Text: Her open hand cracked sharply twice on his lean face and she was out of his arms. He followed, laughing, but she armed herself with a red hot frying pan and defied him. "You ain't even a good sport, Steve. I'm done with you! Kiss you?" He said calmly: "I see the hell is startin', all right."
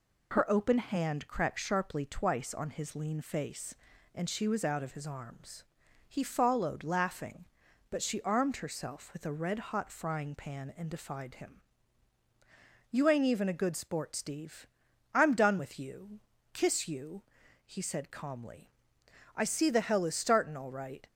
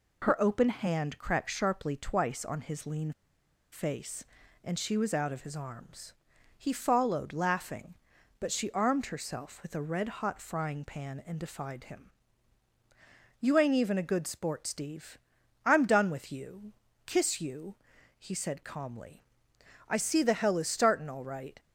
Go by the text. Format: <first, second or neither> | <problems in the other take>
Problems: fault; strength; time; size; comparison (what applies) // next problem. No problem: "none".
first | pauses between "lean" and "face"; noticeable; at 3.1 s; 0.61 s long